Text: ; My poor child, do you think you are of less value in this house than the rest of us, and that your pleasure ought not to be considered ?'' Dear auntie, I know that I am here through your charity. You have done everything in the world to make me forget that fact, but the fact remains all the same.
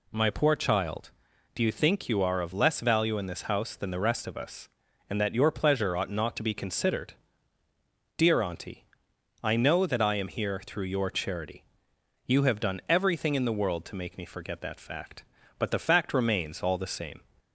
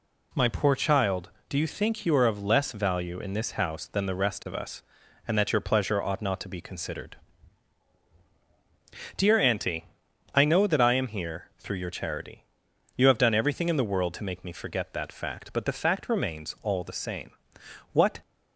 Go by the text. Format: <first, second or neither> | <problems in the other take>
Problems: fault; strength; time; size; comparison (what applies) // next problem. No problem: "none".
first | goes on to say "What"; slight; from 17.9 s on; 0.26 s long